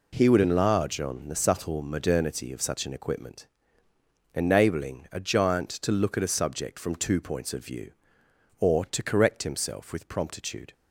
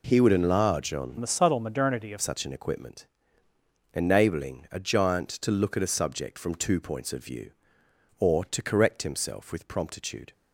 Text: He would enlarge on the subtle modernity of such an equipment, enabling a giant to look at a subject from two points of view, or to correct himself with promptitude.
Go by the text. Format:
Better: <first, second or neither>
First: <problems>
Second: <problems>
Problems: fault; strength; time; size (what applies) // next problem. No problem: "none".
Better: first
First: none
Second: changes voice from "the" to "of"; from 1.1 to 2.1 s; 1.0 s long